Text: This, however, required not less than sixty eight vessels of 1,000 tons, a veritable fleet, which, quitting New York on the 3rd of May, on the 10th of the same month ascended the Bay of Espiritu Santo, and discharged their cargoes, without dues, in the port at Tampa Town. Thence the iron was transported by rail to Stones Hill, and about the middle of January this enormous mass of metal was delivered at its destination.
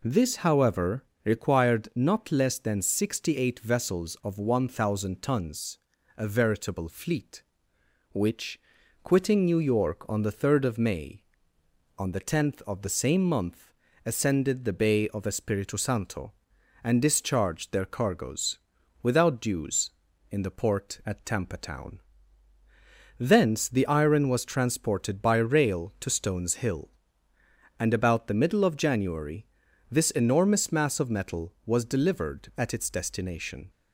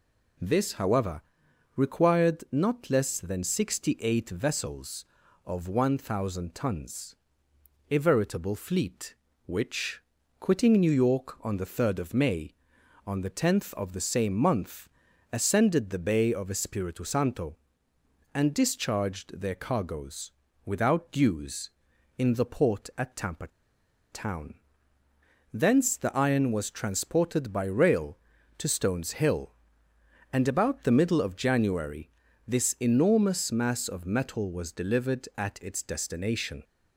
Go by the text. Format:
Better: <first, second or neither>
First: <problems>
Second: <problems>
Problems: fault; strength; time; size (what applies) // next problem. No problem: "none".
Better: first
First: pauses between "month" and "ascended"; slight; at 13.7 s; 0.32 s long // pauses between "January" and "this"; at 29.4 s; 0.42 s long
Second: pauses between "month" and "ascended"; at 14.8 s; 0.42 s long // pauses between "Tampa" and "Town"; noticeable; at 23.4 s; 0.64 s long // pauses between "January" and "this"; at 32.0 s; 0.38 s long